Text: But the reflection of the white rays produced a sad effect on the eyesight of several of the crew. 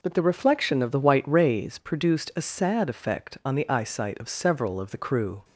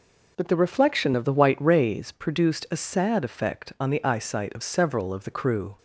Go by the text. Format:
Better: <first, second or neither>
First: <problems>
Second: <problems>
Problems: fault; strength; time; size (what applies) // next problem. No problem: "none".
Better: neither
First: none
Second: none